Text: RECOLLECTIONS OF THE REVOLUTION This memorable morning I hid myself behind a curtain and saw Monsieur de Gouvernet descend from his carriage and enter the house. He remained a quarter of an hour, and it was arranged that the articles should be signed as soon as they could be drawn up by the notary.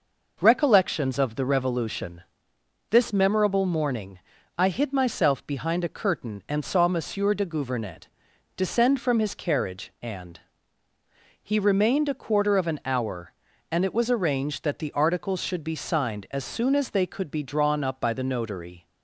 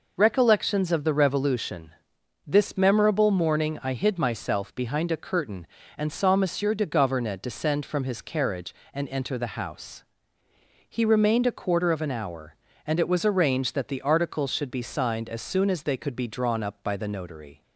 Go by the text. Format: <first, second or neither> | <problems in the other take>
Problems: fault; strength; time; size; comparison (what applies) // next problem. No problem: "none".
second | pauses between "REVOLUTION" and "This"; noticeable; at 2.2 s; 0.70 s long; noticeable in the second // pauses between "morning" and "I"; slight; at 4.1 s; 0.36 s long // pauses between "Gouvernet" and "descend"; noticeable; at 8.0 s; 0.50 s long // skips "enter the house"; at 10.8 s